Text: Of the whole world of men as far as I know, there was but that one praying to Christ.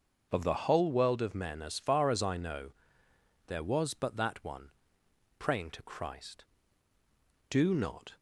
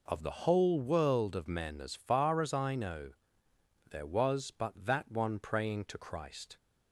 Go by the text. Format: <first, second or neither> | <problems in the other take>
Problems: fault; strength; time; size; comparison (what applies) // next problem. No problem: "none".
second | starts louder than the rest; until 1.3 s; 6.5 dB // pauses between "one" and "praying"; noticeable; at 4.7 s; 0.68 s long // goes on to say "Do not"; noticeable; from 7.4 s on; 0.68 s long